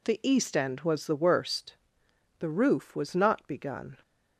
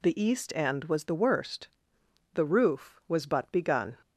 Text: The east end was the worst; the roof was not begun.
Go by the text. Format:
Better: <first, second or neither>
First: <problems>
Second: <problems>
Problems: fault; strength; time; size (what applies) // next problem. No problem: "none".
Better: first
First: none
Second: says "but" for "not"; at 3.2 s